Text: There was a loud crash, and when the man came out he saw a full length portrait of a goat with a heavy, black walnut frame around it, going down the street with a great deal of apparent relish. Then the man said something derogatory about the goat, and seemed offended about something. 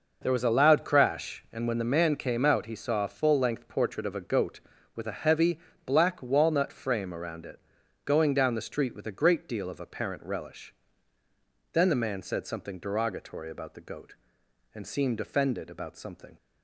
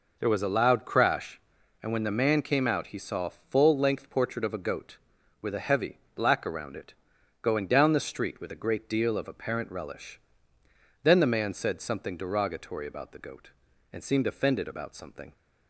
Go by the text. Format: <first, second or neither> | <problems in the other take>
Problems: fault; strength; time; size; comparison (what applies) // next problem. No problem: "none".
first | skips "walnut frame"; at 6.4 s